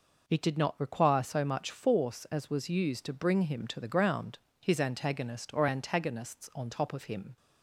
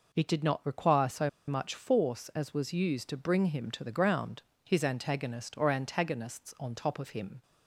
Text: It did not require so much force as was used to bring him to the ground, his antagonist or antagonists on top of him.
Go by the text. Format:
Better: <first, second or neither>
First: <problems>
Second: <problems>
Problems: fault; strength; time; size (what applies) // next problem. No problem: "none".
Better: first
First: none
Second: pauses between "so" and "much"; slight; at 1.2 s; 0.18 s long